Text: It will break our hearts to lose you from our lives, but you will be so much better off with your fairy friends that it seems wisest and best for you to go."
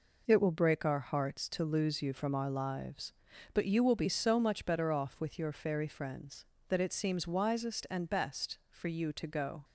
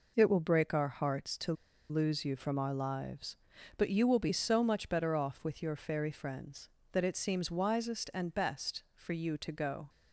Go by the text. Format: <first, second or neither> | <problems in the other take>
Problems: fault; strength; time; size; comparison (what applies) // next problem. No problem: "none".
first | pauses between "to" and "lose"; at 1.5 s; 0.36 s long